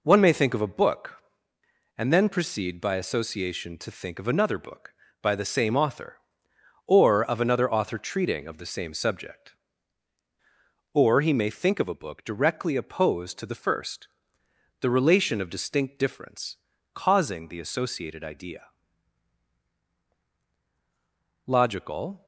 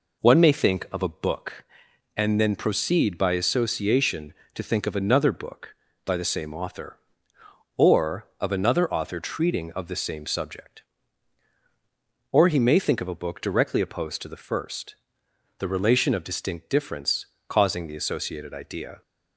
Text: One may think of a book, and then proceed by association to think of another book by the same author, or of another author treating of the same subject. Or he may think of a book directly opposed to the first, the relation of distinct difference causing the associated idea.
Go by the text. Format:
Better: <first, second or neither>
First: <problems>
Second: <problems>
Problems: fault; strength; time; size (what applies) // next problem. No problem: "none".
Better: second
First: pauses between "difference" and "causing"; at 16.5 s; 0.38 s long // goes on to say "Logical"; noticeable; from 21.4 s on; 0.80 s long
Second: pauses between "difference" and "causing"; slight; at 17.2 s; 0.22 s long